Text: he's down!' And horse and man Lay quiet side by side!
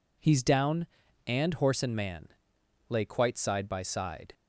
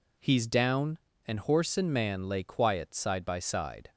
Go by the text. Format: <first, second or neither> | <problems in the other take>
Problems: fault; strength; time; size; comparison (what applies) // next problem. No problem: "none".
second | pauses between "man" and "Lay"; noticeable; at 2.2 s; 0.60 s long // says "quite" for "quiet"; at 3.0 s